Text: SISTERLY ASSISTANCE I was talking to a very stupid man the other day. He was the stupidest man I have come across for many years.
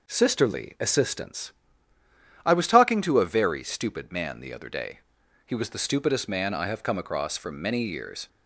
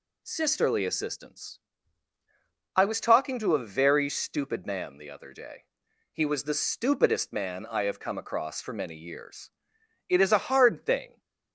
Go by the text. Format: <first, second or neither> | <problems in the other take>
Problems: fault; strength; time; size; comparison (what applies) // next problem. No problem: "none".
first | pauses between "ASSISTANCE" and "I"; at 1.5 s; 1.1 s long; noticeable in the first // goes on to say "It is a hard thing"; noticeable; from 10.0 s on; 1.1 s long